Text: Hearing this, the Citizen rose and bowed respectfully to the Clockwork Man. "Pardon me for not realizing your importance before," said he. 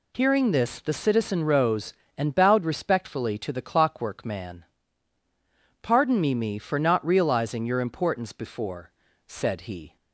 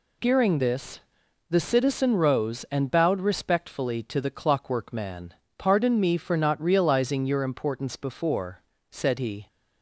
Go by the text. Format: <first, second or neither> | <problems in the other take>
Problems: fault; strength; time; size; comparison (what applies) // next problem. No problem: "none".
second | says "me" twice; at 6.3 s